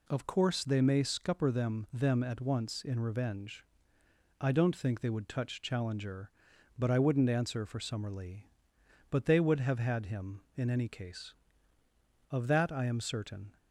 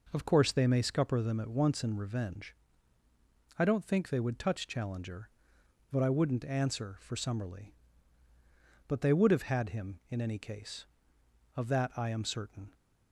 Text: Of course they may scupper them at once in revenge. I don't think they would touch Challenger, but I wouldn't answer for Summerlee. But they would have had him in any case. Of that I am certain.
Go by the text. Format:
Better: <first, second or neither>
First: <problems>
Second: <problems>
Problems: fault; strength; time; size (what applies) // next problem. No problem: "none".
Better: second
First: says "them" twice; at 1.9 s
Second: none